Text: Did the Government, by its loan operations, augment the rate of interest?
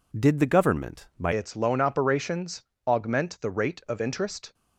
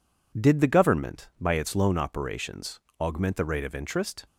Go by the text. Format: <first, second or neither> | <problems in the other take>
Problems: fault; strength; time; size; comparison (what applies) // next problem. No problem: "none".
second | changes voice at "its"; from 1.3 s on; 3.2 s long